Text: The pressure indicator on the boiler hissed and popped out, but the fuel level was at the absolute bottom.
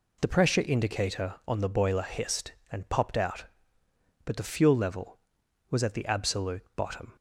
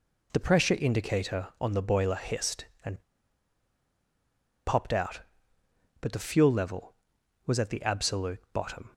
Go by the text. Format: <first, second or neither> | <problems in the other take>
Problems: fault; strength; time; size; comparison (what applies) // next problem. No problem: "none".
first | pauses between "and" and "popped"; strong; at 3.0 s; 1.6 s long